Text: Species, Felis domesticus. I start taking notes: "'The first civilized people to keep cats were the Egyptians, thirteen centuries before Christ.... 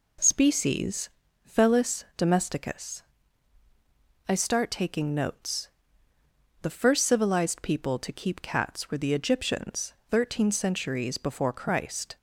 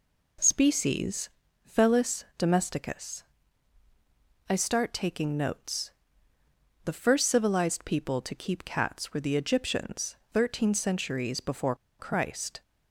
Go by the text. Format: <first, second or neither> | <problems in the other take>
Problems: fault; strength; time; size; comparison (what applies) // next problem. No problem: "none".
first | pauses between "before" and "Christ"; slight; at 11.7 s; 0.23 s long